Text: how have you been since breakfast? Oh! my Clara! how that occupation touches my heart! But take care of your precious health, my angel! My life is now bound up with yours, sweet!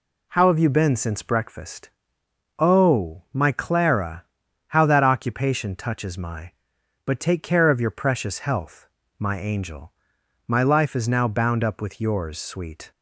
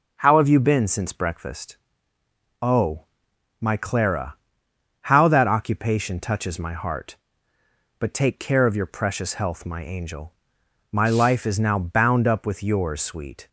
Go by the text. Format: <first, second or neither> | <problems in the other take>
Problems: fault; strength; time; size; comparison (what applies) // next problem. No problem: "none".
second | skips "heart"; at 6.7 s